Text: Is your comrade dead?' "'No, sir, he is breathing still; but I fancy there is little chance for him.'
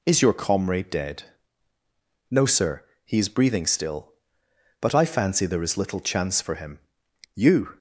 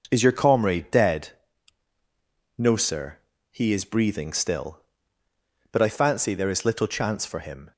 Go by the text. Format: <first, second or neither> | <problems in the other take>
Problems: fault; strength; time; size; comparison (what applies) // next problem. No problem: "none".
second | goes on to say "You"; slight; from 7.3 s on; 0.42 s long